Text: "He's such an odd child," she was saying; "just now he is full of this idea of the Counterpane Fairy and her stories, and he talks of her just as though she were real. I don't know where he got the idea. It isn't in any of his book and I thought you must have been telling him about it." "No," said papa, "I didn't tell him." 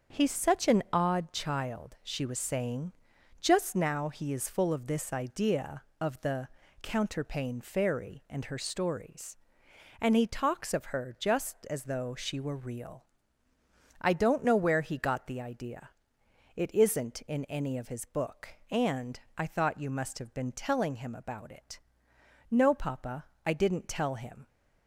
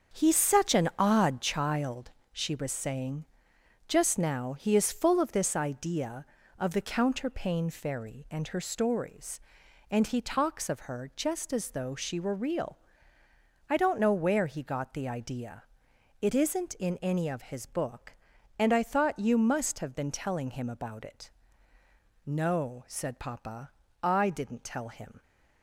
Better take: second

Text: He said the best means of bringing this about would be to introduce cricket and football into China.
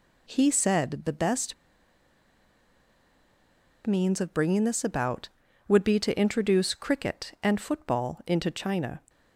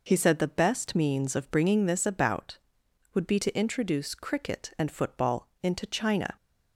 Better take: second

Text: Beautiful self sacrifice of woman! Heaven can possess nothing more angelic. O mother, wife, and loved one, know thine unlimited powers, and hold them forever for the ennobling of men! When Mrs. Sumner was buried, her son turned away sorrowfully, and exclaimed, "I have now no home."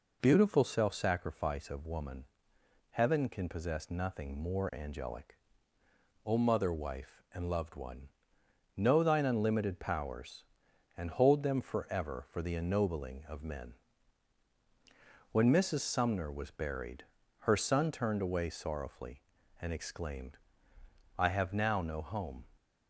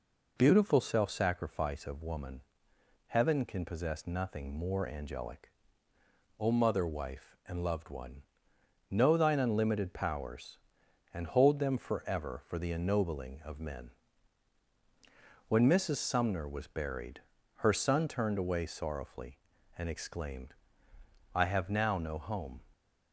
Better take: neither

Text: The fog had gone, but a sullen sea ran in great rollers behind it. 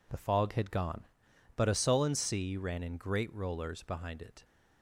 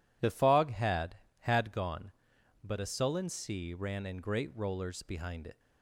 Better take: first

